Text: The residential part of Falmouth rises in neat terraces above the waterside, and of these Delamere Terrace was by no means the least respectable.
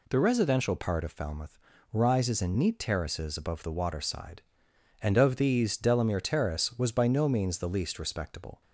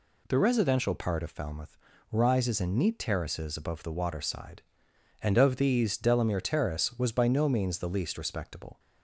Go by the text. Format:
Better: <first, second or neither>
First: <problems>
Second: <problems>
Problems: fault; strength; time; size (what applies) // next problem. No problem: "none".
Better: neither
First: pauses between "Falmouth" and "rises"; slight; at 1.5 s; 0.34 s long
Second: pauses between "Falmouth" and "rises"; slight; at 1.7 s; 0.34 s long